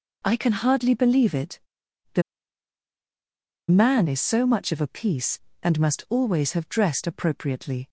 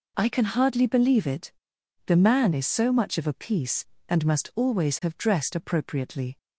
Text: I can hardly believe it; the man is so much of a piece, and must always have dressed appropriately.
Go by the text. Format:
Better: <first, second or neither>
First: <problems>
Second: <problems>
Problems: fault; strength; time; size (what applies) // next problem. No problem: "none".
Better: second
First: pauses between "the" and "man"; strong; at 2.2 s; 1.4 s long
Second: none